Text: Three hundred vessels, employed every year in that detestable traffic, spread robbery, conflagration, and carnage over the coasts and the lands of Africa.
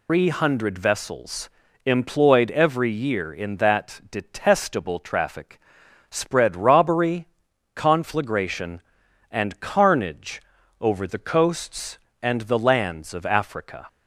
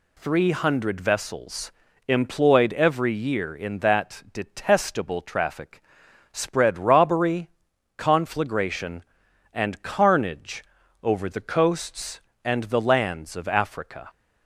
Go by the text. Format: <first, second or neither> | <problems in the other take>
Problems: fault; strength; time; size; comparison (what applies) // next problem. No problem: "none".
second | loses the start of "Three"; at 0.0 s; 150 ms // pauses between "carnage" and "over"; at 10.4 s; 0.40 s long; also in the second